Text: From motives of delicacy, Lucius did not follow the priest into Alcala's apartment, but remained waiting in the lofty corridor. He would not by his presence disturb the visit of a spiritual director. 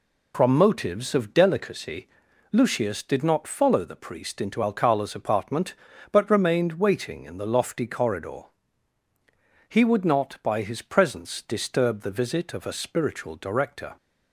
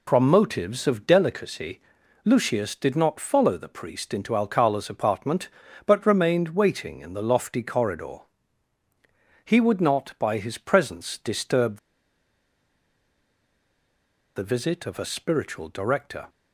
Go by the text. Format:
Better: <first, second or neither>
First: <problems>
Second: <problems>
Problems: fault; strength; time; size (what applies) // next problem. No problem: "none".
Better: first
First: none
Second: pauses between "disturb" and "the"; strong; at 11.7 s; 2.5 s long